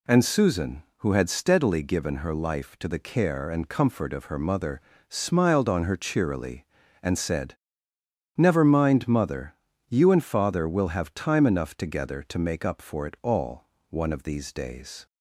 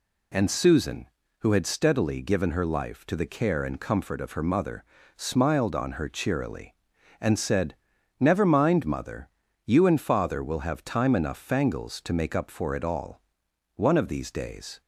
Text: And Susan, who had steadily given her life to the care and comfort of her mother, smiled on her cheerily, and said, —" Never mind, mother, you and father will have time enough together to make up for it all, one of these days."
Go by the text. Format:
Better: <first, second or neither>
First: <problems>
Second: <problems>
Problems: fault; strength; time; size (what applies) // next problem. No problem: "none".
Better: first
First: none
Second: says "fangles" for "together"; at 11.3 s